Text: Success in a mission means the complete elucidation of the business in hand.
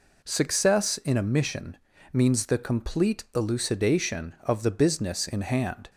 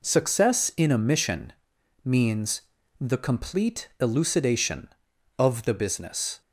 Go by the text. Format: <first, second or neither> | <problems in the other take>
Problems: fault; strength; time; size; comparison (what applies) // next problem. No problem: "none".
first | pauses between "mission" and "means"; noticeable; at 1.5 s; 0.50 s long; slight in the first // pauses between "means" and "the"; slight; at 2.6 s; 0.36 s long // stops before "in hand"; at 6.4 s